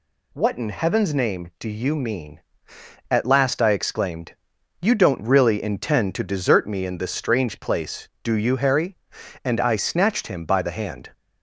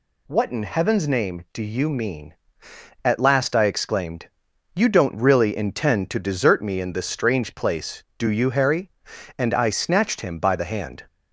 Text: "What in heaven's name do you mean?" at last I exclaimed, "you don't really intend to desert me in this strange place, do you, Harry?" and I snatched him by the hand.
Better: neither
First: none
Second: none

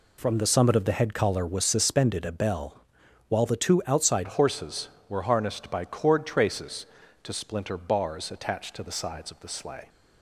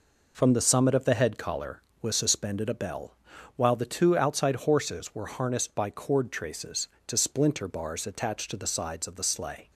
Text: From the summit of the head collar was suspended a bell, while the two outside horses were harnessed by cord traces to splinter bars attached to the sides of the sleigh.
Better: second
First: changes voice at "horses"; from 4.2 s on; 5.6 s long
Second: none

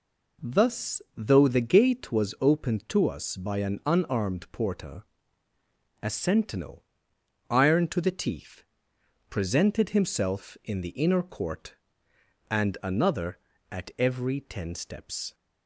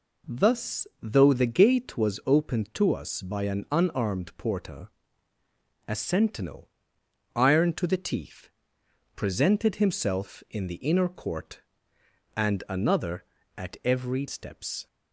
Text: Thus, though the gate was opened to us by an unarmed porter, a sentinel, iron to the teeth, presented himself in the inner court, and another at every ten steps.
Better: first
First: none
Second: skips "ten"; at 14.2 s

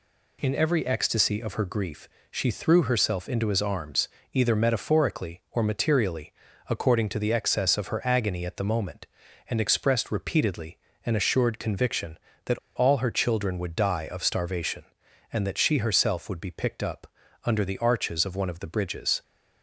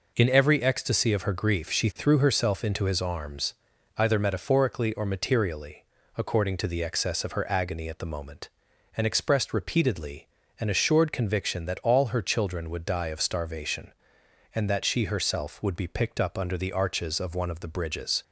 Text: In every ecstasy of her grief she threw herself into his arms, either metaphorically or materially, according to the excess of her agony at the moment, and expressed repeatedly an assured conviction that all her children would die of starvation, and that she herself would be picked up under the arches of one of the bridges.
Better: second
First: pauses between "grief" and "she"; slight; at 2.0 s; 0.22 s long // pauses between "repeatedly" and "an"; slight; at 10.7 s; 0.26 s long // pauses between "that" and "all"; slight; at 12.5 s; 0.17 s long // pauses between "up" and "under"; at 17.0 s; 0.38 s long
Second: pauses between "repeatedly" and "an"; slight; at 10.2 s; 0.32 s long

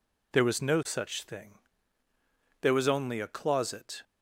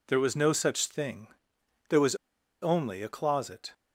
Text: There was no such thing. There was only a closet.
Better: first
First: none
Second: pauses between "was" and "only"; at 2.1 s; 0.45 s long

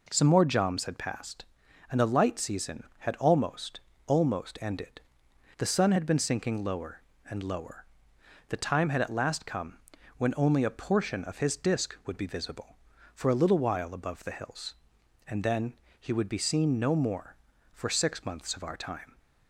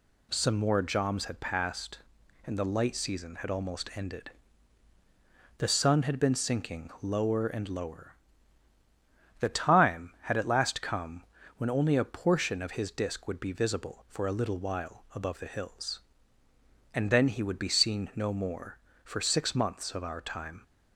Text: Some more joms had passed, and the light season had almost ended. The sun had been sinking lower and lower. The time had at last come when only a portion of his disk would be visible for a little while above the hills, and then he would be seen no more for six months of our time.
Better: second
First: says "almost" twice; at 4.0 s // pauses between "come" and "when"; slight; at 9.7 s; 0.36 s long // pauses between "then" and "he"; slight; at 15.7 s; 0.26 s long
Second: pauses between "come" and "when"; slight; at 11.2 s; 0.34 s long

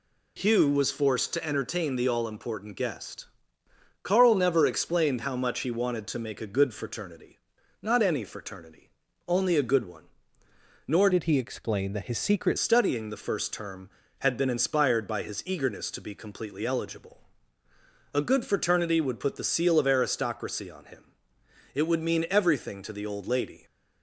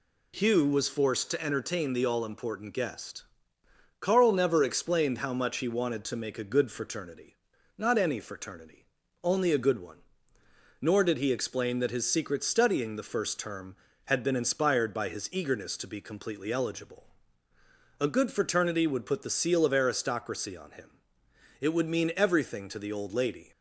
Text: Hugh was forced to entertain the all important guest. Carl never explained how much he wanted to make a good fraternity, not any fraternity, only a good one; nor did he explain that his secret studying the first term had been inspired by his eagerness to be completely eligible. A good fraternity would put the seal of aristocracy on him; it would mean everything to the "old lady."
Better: second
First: changes voice from "did" to "secret"; from 11.1 to 12.5 s; 1.4 s long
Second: none

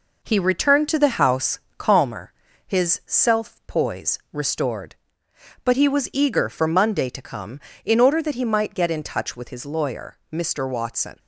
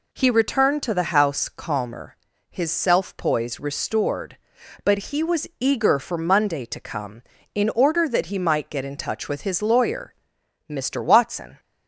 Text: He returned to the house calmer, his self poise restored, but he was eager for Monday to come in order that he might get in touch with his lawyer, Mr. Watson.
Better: second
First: gets quieter; noticeable; throughout; 4.5 dB // pauses between "house" and "calmer"; slight; at 1.5 s; 0.20 s long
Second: none

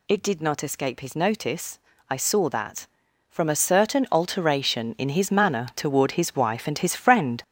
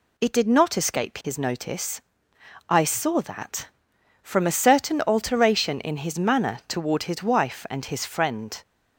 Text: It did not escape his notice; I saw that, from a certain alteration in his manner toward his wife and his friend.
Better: second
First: gets louder; throughout; 6.5 dB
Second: none

